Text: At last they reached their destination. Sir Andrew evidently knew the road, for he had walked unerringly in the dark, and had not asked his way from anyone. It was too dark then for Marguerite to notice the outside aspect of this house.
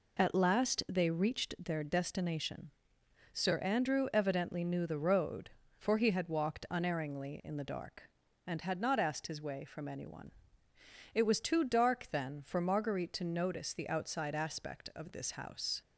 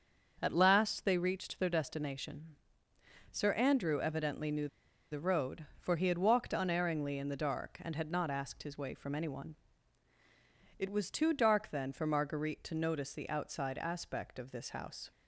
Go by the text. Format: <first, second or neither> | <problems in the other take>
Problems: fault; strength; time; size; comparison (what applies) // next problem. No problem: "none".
first | starts louder than the rest; until 1.4 s; 6.5 dB // pauses between "knew" and "the"; at 4.6 s; 0.42 s long